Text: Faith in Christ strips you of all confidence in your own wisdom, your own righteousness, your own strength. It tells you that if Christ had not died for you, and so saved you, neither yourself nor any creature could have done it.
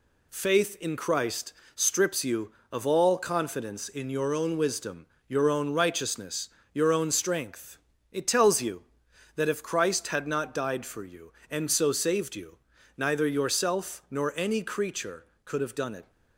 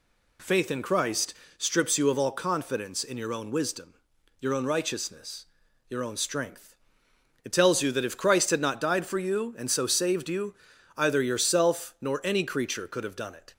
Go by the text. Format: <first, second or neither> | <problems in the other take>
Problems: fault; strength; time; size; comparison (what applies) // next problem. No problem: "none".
first | pauses between "Christ" and "strips"; slight; at 1.3 s; 0.24 s long; slight in the first // says "either" for "neither"; at 10.9 s